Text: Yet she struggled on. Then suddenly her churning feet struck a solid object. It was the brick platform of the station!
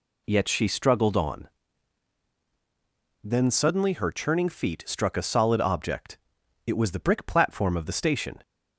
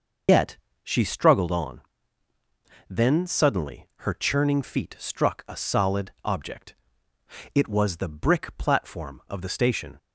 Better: first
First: none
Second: loses the start of "Yet"; at 0.2 s; 90 ms // pauses between "Yet" and "she"; slight; at 0.5 s; 0.26 s long

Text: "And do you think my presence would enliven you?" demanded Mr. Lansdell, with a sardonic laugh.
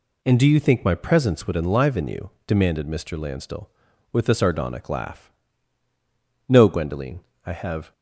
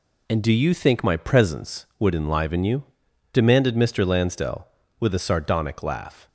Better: second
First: goes on to say "No Gwendoline I have"; from 6.4 s on; 1.4 s long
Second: none

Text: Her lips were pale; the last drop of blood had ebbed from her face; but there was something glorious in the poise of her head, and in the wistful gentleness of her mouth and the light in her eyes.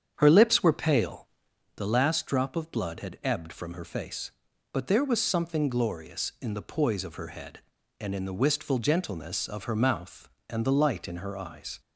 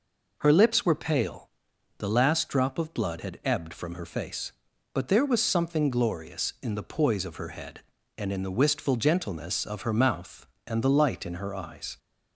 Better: second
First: starts louder than the rest; strong; until 1.7 s; 8 dB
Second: none

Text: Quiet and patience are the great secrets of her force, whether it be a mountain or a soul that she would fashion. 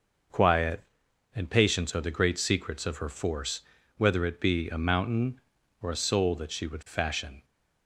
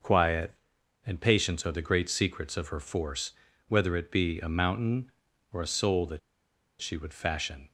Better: first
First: starts louder than the rest; noticeable; until 1.8 s; 6 dB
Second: starts louder than the rest; noticeable; until 1.5 s; 6 dB // pauses between "that" and "she"; noticeable; at 6.1 s; 0.61 s long

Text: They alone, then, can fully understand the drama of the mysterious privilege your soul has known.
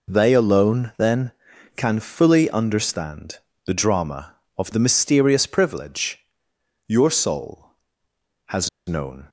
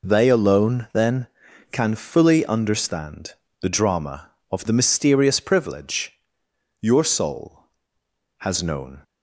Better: second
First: pauses between "understand" and "the"; slight; at 3.3 s; 0.30 s long // pauses between "privilege" and "your"; noticeable; at 6.2 s; 0.62 s long // pauses between "has" and "known"; slight; at 8.6 s; 0.19 s long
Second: pauses between "understand" and "the"; slight; at 3.3 s; 0.30 s long // pauses between "privilege" and "your"; noticeable; at 6.1 s; 0.62 s long

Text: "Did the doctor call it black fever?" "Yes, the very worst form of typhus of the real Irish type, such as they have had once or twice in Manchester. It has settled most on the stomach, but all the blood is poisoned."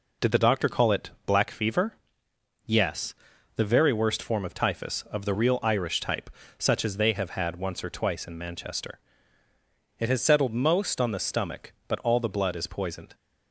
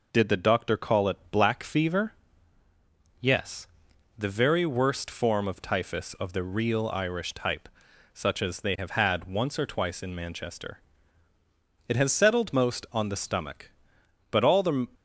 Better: first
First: none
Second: stops before "blood is poisoned"; at 14.9 s

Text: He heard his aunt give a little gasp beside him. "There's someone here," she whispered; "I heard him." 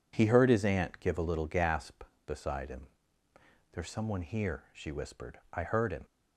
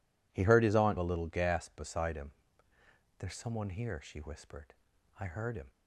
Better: first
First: none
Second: skips "give"; at 0.9 s

